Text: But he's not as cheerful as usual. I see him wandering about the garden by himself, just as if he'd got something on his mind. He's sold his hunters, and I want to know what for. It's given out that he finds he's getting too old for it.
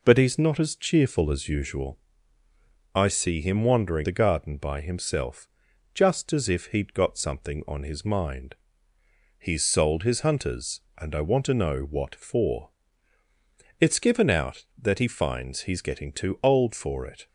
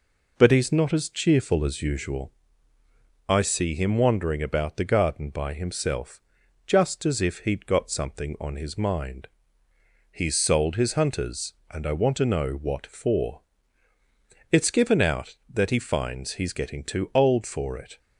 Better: second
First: skips "about"; at 4.0 s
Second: none

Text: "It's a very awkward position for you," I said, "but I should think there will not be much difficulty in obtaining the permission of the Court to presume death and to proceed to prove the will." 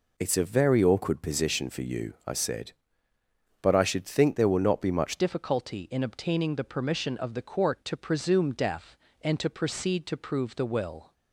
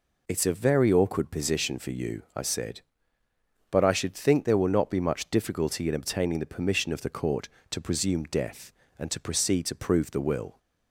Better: second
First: changes voice at "difficulty"; from 5.1 s on; 6.0 s long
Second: none

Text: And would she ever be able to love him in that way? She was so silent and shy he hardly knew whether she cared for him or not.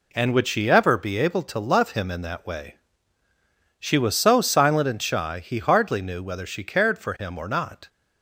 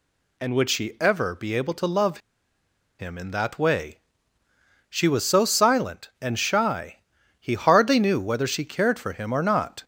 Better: first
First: none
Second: pauses between "love" and "him"; noticeable; at 2.1 s; 0.79 s long // pauses between "shy" and "he"; at 6.9 s; 0.42 s long

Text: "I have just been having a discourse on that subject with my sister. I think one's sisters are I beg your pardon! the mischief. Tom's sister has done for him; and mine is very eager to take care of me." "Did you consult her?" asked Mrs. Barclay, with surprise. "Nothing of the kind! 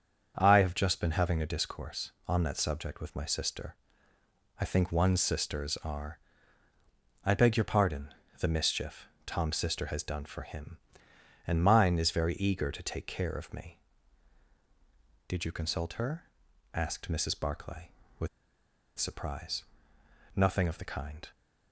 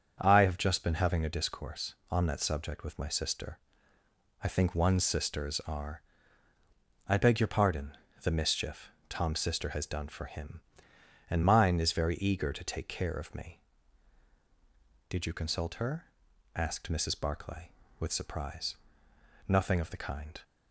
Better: second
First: starts louder than the rest; strong; until 1.3 s; 7 dB // pauses between "are" and "I"; at 6.1 s; 1.0 s long // pauses between "with" and "surprise"; noticeable; at 18.2 s; 0.69 s long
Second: starts louder than the rest; strong; until 1.1 s; 7 dB // pauses between "are" and "I"; at 6.0 s; 1.0 s long

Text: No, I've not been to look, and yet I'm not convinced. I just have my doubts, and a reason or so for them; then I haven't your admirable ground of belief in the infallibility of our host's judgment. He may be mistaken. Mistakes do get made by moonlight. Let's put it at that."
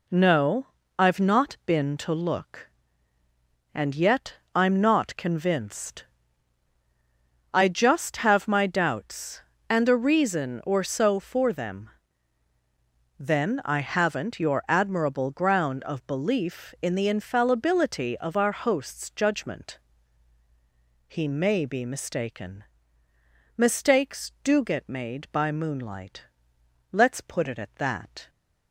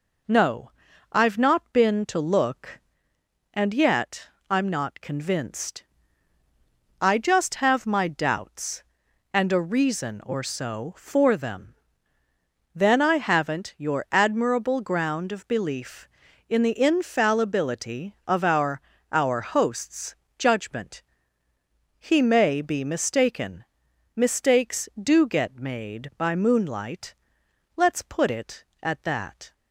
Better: first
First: pauses between "yet" and "I'm"; slight; at 4.3 s; 0.20 s long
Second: pauses between "yet" and "I'm"; slight; at 4.2 s; 0.20 s long // says "our" twice; at 19.1 s // pauses between "host's" and "judgment"; slight; at 20.1 s; 0.24 s long

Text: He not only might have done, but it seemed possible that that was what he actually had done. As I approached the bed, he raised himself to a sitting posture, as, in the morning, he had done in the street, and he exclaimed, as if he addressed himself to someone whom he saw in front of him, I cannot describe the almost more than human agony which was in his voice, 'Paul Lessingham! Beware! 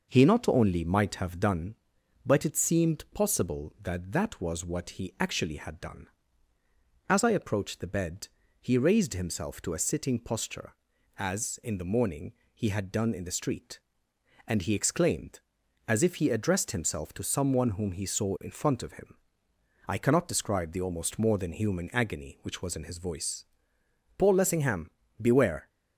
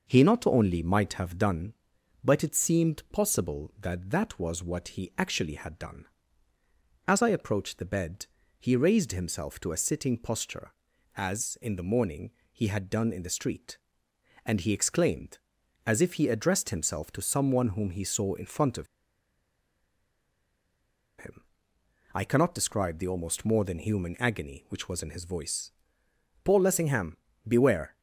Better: first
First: none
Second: pauses between "of" and "him"; strong; at 18.8 s; 2.3 s long

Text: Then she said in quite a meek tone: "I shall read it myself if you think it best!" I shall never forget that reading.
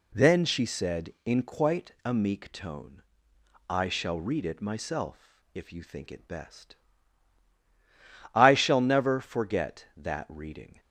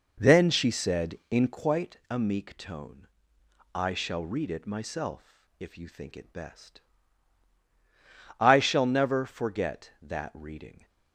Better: first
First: none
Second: starts louder than the rest; noticeable; until 1.7 s; 5 dB

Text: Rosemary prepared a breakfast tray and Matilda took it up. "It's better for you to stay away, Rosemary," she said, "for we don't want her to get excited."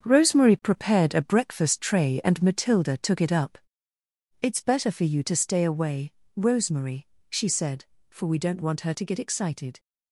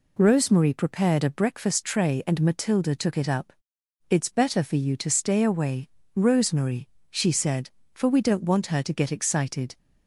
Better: second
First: gets quieter; strong; throughout; 8.5 dB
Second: none

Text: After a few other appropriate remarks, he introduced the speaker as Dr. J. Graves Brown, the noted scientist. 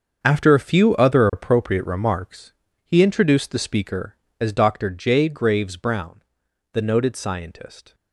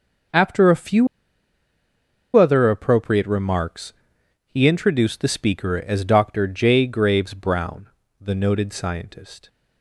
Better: first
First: starts louder than the rest; until 1.2 s; 7 dB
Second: starts louder than the rest; until 2.6 s; 6 dB // pauses between "few" and "other"; strong; at 1.0 s; 1.2 s long

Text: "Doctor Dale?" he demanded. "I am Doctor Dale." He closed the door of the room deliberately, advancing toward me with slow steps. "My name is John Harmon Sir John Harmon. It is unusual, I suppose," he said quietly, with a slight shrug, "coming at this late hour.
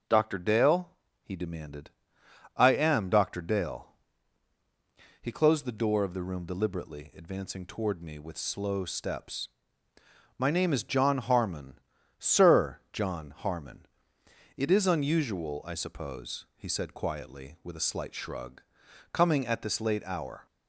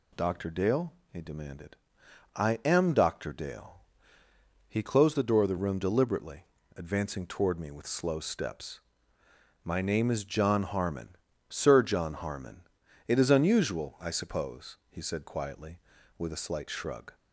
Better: first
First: pauses between "Harmon" and "Sir"; at 11.7 s; 0.40 s long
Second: pauses between "Harmon" and "Sir"; slight; at 11.1 s; 0.32 s long // stops before "coming at this late hour"; at 17.1 s

